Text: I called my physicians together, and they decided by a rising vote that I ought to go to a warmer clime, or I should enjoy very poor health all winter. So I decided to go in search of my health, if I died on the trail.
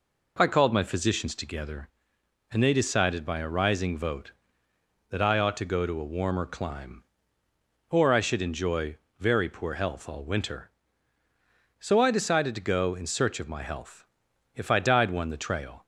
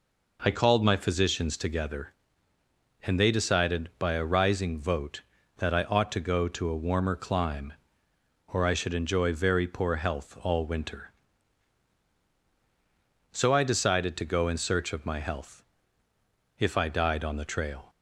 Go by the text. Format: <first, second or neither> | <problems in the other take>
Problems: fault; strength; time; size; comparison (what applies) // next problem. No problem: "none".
second | pauses between "enjoy" and "very"; slight; at 8.9 s; 0.20 s long // says "one" for "on"; at 15.0 s